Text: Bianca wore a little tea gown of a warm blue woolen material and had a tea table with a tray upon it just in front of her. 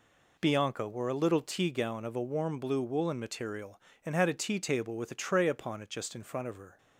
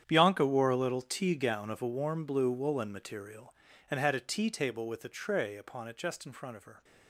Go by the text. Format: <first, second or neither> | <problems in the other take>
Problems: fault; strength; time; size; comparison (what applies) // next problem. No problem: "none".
first | gets quieter; strong; throughout; 14.5 dB